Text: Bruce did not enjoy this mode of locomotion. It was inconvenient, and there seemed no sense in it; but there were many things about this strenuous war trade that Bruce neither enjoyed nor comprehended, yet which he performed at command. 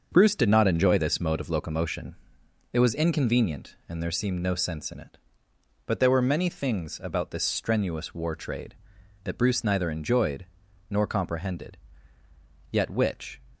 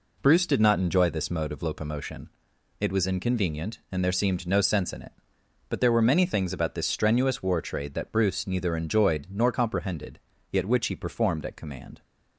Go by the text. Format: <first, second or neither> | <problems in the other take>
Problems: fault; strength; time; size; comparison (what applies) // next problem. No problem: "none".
second | starts louder than the rest; until 1.1 s; 6.5 dB // pauses between "enjoyed" and "nor"; noticeable; at 10.4 s; 0.46 s long // stops before "he performed at command"; at 13.5 s